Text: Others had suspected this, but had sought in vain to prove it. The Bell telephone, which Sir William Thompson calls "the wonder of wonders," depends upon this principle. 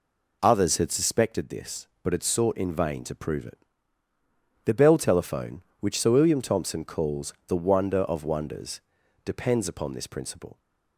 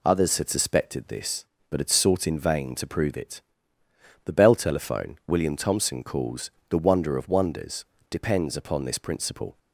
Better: first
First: none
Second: skips "which Sir"; at 5.2 s // pauses between "calls" and "the"; slight; at 6.5 s; 0.20 s long

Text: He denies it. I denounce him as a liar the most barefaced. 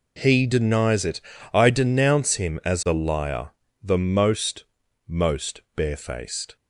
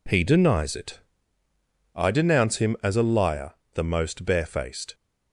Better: second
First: pauses between "liar" and "the"; slight; at 3.5 s; 0.30 s long // says "most" twice; at 5.0 s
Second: pauses between "liar" and "the"; slight; at 3.5 s; 0.20 s long

